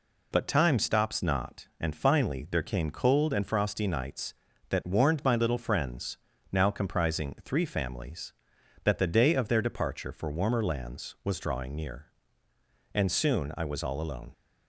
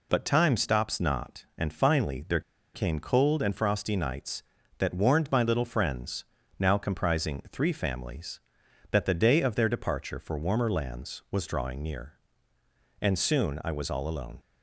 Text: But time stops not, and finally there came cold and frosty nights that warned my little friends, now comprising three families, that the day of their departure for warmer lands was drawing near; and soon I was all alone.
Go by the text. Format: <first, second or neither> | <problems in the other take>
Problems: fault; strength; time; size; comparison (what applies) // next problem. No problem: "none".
first | pauses between "there" and "came"; slight; at 2.4 s; 0.33 s long